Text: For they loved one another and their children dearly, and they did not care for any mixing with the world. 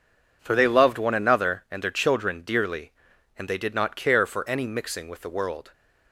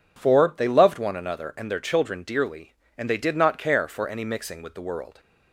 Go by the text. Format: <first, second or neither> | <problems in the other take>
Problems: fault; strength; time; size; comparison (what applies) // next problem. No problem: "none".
neither | none